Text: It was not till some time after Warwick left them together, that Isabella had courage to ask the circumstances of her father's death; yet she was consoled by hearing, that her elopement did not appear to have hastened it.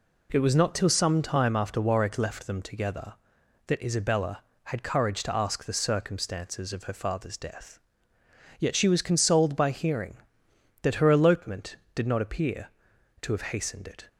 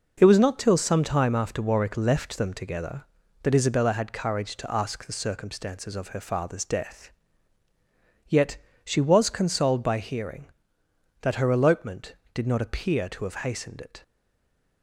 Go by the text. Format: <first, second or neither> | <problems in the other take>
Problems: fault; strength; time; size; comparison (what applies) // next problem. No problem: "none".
first | pauses between "yet" and "she"; slight; at 8.5 s; 0.26 s long // stays silent after the last word; slight; from 14.0 s on; 0.8 s long